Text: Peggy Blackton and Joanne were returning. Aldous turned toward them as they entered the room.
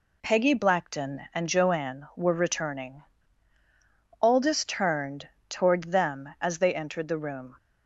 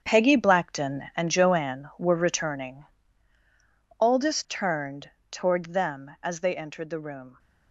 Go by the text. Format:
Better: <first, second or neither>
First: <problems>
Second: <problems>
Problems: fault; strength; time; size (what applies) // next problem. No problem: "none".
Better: first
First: pauses between "turned" and "toward"; slight; at 5.2 s; 0.18 s long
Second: gets quieter; strong; throughout; 10.5 dB // pauses between "turned" and "toward"; slight; at 5.1 s; 0.18 s long